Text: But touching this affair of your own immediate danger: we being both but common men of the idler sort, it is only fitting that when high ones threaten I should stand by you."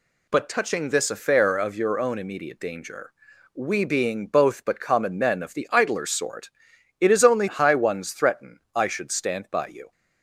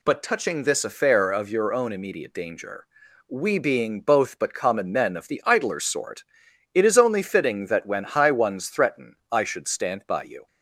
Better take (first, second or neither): second